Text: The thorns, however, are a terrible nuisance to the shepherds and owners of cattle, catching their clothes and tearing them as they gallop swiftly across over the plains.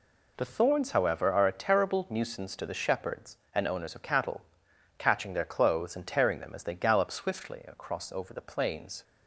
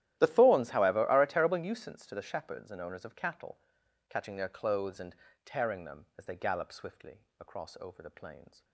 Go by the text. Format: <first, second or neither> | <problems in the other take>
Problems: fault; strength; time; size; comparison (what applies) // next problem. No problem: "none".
first | starts louder than the rest; strong; until 1.7 s; 13 dB // pauses between "and" and "tearing"; slight; at 5.1 s; 0.30 s long // pauses between "swiftly" and "across"; slight; at 7.2 s; 0.20 s long